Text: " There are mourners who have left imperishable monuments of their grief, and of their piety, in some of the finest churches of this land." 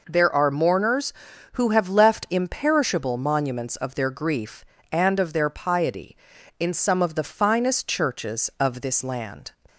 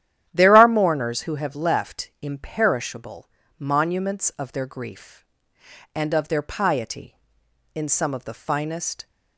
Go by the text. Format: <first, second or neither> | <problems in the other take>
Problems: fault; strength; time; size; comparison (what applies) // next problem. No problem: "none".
first | starts louder than the rest; strong; until 1.2 s; 11 dB // pauses between "imperishable" and "monuments"; slight; at 3.3 s; 0.28 s long // stops before "churches of this land"; at 9.0 s